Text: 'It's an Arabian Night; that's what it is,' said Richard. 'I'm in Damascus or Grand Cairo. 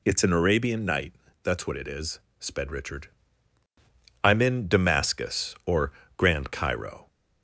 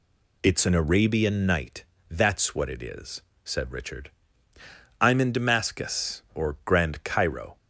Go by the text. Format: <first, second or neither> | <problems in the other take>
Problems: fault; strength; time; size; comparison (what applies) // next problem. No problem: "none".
second | says "sped" for "said"; at 2.3 s // pauses between "or" and "Grand"; slight; at 5.9 s; 0.26 s long